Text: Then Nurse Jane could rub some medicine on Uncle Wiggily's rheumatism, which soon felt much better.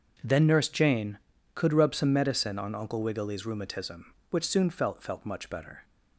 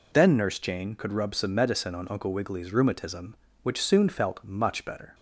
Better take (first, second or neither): second